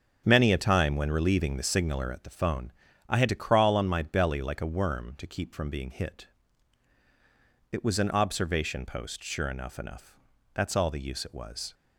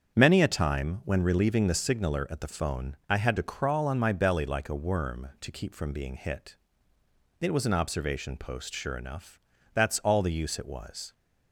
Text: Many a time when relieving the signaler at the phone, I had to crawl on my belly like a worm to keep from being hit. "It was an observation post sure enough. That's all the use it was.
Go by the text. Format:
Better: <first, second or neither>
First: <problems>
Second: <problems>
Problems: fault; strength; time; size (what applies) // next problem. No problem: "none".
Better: second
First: starts louder than the rest; strong; until 1.2 s; 7.5 dB // says "enough" twice; at 9.7 s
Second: starts louder than the rest; strong; until 1.1 s; 7.5 dB